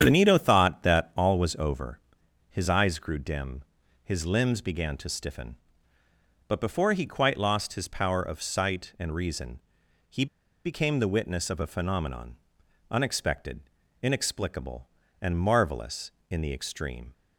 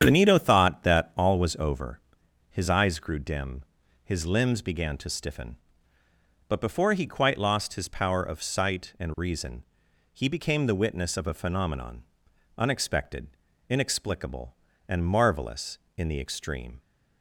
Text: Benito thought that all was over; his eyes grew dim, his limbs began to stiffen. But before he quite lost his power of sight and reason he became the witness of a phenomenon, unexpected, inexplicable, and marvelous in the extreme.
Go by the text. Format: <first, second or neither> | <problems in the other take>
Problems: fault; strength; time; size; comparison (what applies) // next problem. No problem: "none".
second | starts louder than the rest; strong; until 1.0 s; 8.5 dB; strong in the second // pauses between "reason" and "he"; noticeable; at 9.5 s; 0.50 s long; noticeable in the second // pauses between "he" and "became"; at 10.2 s; 0.39 s long